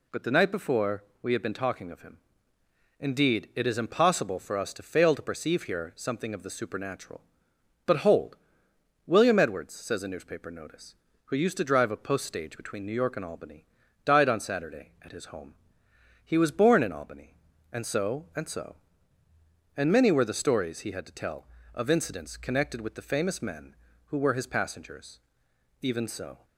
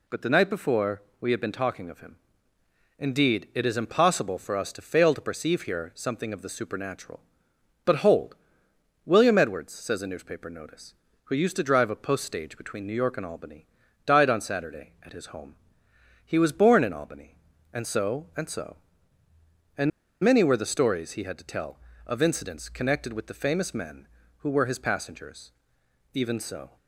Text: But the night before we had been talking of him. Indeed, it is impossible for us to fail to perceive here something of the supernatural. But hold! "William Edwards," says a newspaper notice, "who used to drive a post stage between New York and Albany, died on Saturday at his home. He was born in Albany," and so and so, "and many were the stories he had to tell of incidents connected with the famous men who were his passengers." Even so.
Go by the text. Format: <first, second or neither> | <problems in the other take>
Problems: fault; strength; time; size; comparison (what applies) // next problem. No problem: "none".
first | pauses between "before" and "we"; slight; at 1.0 s; 0.18 s long; slight in the first // pauses between "and" and "many"; slight; at 19.9 s; 0.32 s long